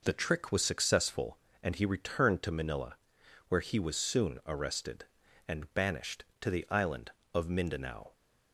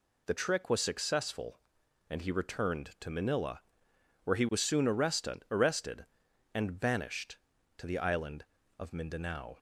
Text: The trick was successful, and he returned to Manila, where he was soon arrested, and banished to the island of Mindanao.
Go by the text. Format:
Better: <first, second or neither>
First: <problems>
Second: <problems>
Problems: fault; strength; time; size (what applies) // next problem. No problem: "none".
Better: first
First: none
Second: says "arrested" twice; at 5.5 s